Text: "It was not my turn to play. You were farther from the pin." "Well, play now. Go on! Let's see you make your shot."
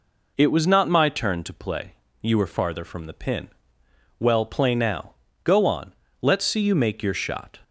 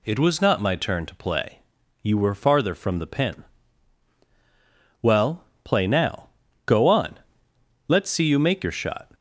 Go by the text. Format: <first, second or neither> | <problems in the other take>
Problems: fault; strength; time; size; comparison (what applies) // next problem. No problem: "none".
neither | none